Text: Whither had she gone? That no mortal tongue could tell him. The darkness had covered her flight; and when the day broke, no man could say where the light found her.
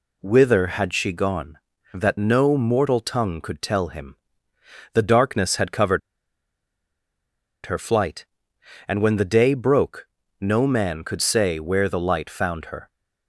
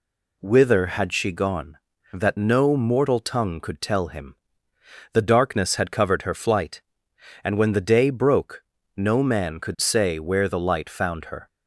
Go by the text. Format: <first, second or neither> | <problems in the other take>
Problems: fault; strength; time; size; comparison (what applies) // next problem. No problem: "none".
second | pauses between "covered" and "her"; strong; at 6.0 s; 1.6 s long